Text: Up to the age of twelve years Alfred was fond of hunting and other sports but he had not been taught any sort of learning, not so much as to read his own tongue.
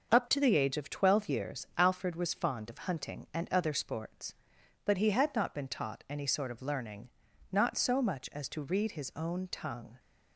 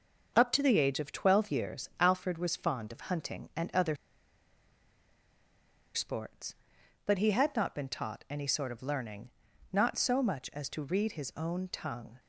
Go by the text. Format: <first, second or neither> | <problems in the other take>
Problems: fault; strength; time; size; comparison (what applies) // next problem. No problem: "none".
first | starts louder than the rest; until 1.3 s; 6 dB; also in the first // pauses between "other" and "sports"; strong; at 3.9 s; 1.9 s long